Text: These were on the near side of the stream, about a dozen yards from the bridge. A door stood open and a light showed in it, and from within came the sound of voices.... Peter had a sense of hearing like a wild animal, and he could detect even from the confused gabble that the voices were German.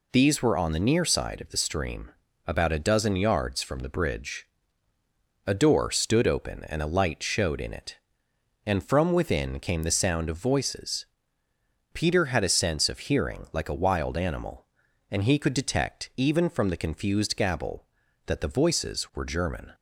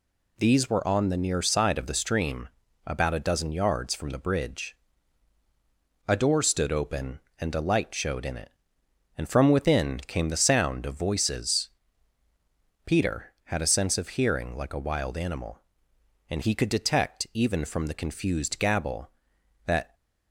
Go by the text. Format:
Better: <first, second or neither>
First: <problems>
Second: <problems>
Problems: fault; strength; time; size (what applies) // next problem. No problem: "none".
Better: first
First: none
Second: stops before "the voices were German"; at 19.9 s